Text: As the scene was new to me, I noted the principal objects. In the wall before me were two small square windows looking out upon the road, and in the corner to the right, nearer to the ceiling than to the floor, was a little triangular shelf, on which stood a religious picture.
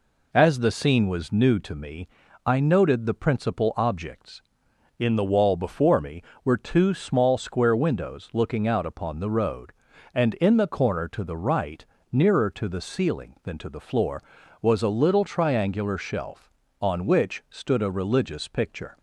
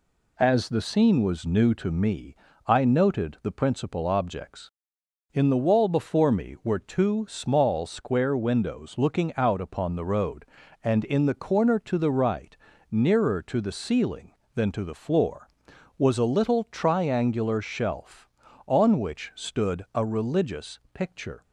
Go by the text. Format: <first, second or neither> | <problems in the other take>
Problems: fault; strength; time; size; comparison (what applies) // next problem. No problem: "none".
neither | none